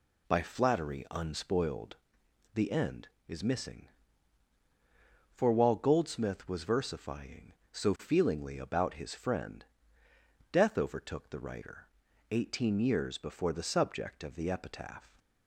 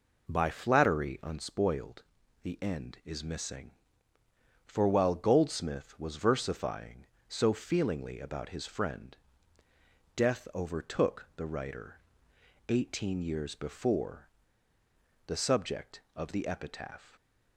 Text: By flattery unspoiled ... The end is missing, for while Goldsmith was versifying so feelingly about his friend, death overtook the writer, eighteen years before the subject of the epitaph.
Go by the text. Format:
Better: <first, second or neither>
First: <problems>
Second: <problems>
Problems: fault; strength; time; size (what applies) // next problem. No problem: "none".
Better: first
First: none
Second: pauses between "before" and "the"; at 14.2 s; 0.98 s long